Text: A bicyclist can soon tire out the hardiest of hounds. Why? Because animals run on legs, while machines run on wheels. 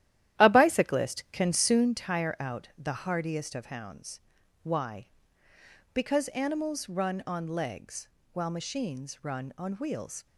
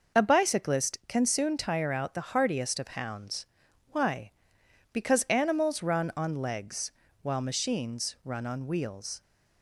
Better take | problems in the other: second | starts louder than the rest; strong; until 1.9 s; 12.5 dB

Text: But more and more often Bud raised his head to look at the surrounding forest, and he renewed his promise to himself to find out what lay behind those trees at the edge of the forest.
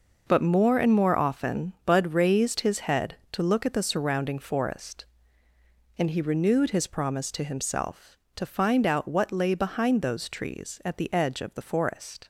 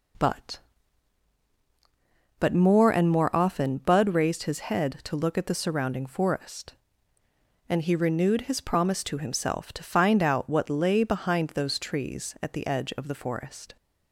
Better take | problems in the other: first | says "But" twice; at 2.3 s

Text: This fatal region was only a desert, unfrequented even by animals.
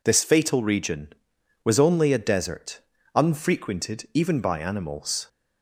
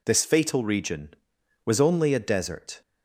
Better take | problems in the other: first | stops before "unfrequented even by animals"; at 2.8 s

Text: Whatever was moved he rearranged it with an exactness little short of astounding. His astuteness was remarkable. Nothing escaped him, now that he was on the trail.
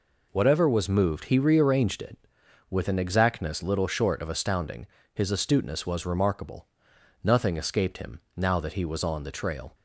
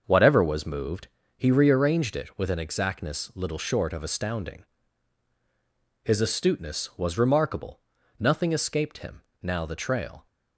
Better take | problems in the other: first | starts louder than the rest; until 1.0 s; 6.5 dB // pauses between "moved" and "he"; slight; at 1.0 s; 0.28 s long // skips "that he was on"; at 9.6 s

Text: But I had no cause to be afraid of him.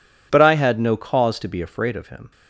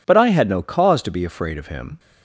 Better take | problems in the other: neither | none

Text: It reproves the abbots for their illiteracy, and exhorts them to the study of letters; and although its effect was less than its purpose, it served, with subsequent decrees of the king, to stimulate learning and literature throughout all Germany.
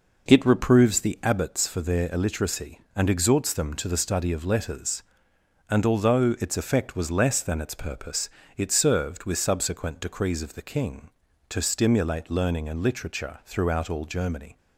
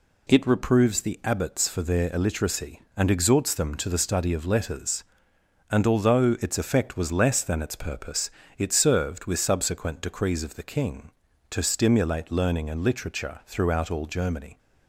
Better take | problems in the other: second | starts louder than the rest; noticeable; until 1.6 s; 5 dB

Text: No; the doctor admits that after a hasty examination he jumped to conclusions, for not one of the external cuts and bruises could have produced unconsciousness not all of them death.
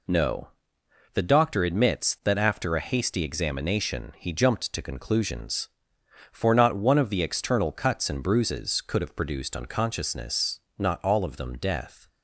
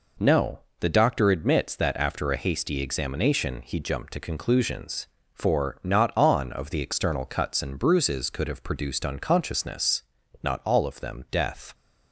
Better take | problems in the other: first | says "on" for "one"; at 6.1 s // pauses between "unconsciousness" and "not"; at 10.0 s; 0.38 s long; slight in the first

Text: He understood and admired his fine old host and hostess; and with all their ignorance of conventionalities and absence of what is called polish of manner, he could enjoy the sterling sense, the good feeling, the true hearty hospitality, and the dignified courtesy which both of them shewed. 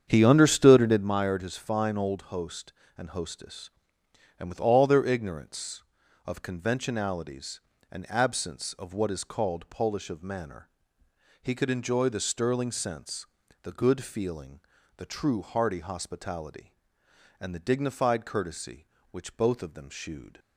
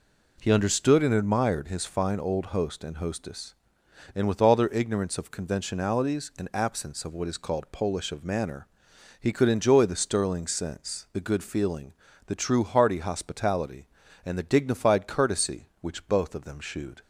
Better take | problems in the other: second | starts louder than the rest; strong; until 1.1 s; 8 dB

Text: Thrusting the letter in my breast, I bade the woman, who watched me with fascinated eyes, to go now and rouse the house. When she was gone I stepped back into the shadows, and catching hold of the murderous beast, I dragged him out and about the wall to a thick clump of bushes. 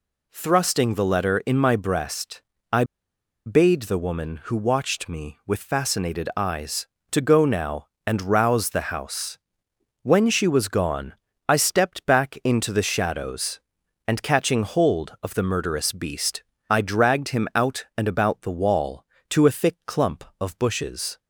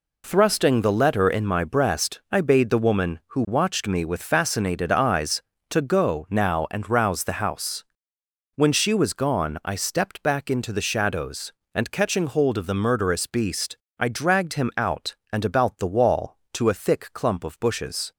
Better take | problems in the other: second | pauses between "I" and "bade"; noticeable; at 2.8 s; 0.62 s long // pauses between "gone" and "I"; slight; at 11.1 s; 0.34 s long

